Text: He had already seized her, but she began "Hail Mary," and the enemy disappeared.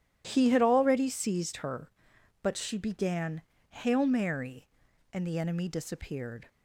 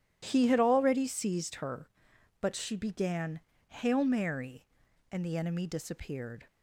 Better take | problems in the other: neither | pauses between "began" and "Hail"; slight; the same in both

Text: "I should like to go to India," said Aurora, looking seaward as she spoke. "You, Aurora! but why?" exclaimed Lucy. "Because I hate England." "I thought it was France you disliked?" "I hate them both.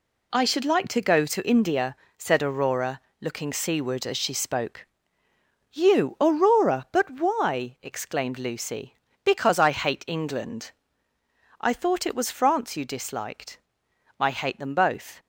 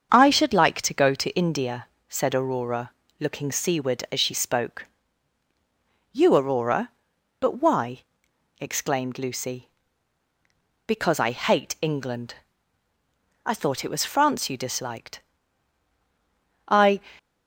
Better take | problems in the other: first | starts louder than the rest; strong; until 1.1 s; 7 dB // stops before "hate them both"; at 17.1 s

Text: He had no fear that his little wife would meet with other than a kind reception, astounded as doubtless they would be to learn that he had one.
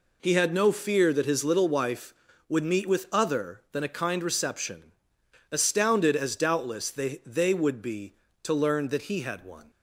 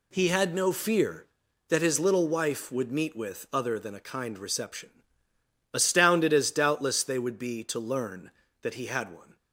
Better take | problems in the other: second | says "they" twice; at 7.2 s

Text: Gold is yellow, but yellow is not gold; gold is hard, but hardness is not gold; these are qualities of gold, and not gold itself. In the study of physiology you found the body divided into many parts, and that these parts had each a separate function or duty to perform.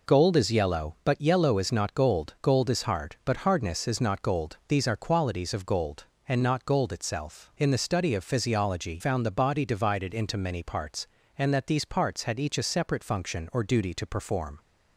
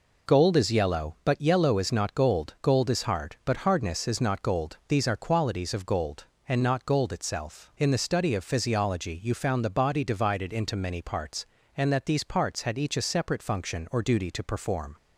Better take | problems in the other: second | skips "you"; at 8.9 s

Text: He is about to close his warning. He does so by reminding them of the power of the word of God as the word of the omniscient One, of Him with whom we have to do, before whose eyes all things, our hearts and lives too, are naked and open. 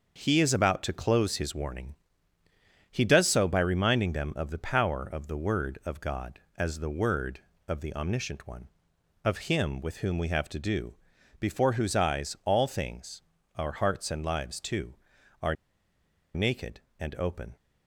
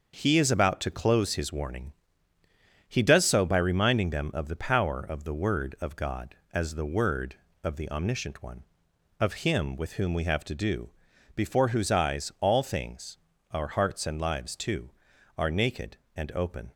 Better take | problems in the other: second | starts louder than the rest; until 1.2 s; 6.5 dB; also in the second // pauses between "are" and "naked"; noticeable; at 15.5 s; 0.81 s long

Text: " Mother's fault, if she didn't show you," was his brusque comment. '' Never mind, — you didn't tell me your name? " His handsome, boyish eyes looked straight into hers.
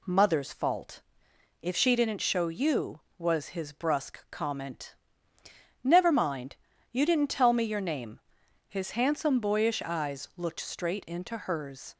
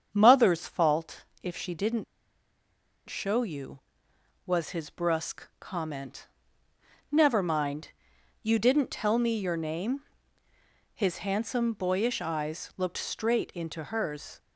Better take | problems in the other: first | starts louder than the rest; strong; until 1.1 s; 8 dB // pauses between "didn't" and "show"; at 2.0 s; 1.0 s long

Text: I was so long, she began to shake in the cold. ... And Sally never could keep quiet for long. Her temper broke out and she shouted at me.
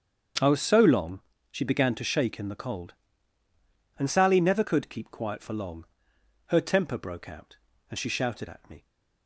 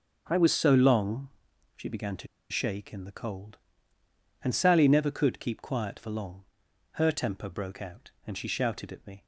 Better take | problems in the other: first | starts louder than the rest; until 1.2 s; 6.5 dB; strong in the first // pauses between "to" and "shake"; slight; at 2.2 s; 0.24 s long

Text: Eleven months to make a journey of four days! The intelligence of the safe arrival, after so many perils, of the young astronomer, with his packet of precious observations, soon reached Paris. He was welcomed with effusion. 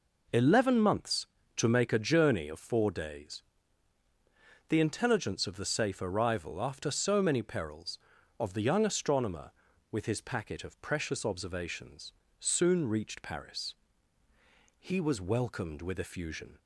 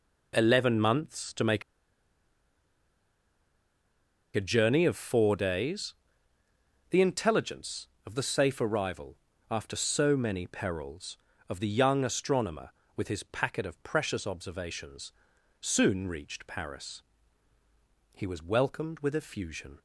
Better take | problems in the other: first | pauses between "make" and "a"; strong; at 1.6 s; 2.7 s long

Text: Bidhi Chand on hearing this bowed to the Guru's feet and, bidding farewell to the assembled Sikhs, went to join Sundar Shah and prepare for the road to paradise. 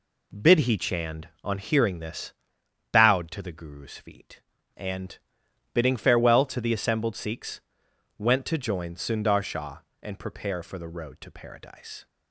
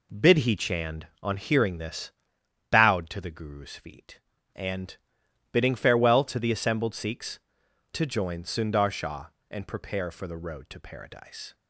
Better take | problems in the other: first | pauses between "this" and "bowed"; noticeable; at 2.1 s; 0.60 s long; noticeable in the first // skips "went"; at 7.6 s

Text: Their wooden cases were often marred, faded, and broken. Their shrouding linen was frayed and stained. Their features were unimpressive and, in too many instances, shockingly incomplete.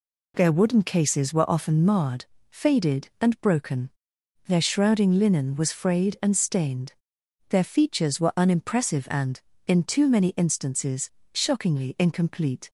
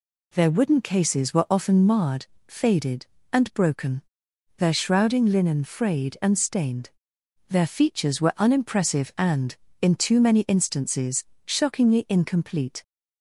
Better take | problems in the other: first | skips "was"; at 5.6 s

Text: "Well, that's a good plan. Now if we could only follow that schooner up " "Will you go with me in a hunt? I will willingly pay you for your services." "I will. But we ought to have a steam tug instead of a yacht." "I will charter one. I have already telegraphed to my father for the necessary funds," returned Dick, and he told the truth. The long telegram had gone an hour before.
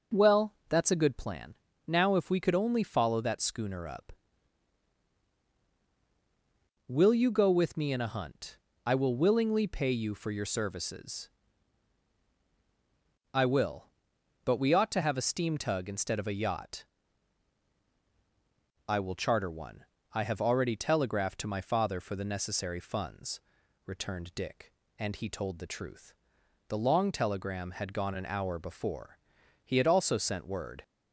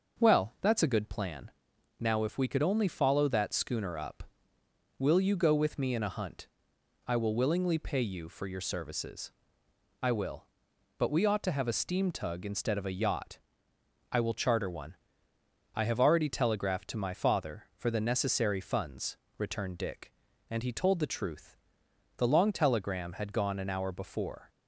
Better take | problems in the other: second | starts louder than the rest; until 1.2 s; 6.5 dB; also in the second // goes on to say "He had also sent word"; noticeable; from 29.6 s on; 1.2 s long

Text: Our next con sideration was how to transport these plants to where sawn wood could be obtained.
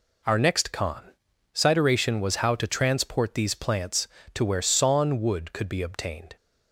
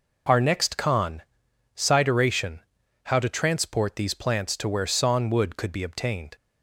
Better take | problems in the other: first | pauses between "con" and "sideration"; noticeable; at 1.2 s; 0.56 s long; noticeable in the first // skips "was"; at 2.8 s

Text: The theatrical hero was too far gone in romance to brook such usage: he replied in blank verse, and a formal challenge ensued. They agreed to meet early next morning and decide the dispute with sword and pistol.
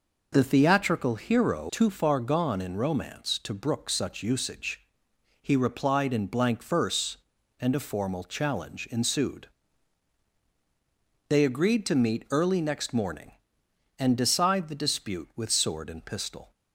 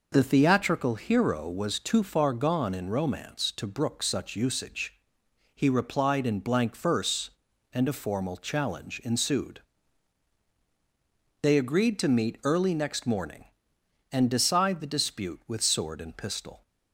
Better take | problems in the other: second | skips "was"; at 1.6 s

